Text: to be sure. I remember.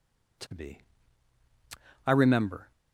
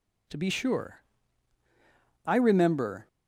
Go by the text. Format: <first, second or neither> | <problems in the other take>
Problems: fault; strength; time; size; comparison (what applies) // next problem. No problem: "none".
second | skips "sure"; at 1.4 s